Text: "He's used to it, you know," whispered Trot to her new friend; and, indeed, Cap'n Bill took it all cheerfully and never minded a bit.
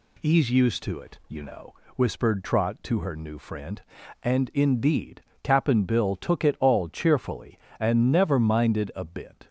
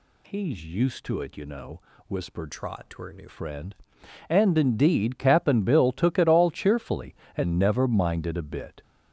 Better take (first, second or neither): first